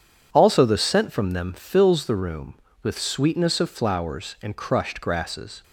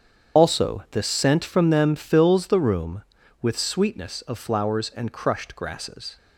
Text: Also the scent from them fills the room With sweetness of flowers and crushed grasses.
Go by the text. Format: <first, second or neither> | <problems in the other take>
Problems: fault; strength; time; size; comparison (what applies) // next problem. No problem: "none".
first | loses the start of "Also"; at 0.3 s; 55 ms // starts louder than the rest; strong; until 1.4 s; 8 dB